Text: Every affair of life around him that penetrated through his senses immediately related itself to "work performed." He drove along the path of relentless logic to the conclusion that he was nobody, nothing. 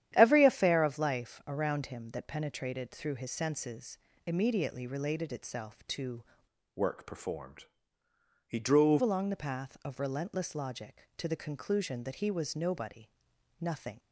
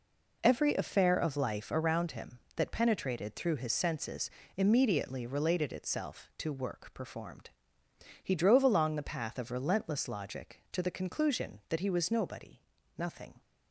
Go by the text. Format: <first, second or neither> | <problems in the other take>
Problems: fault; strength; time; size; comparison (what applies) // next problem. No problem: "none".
second | starts louder than the rest; strong; until 1.1 s; 10.5 dB // pauses between "senses" and "immediately"; slight; at 3.9 s; 0.30 s long; slight in the second // changes voice from "work" to "drove"; from 6.7 to 9.0 s; 2.3 s long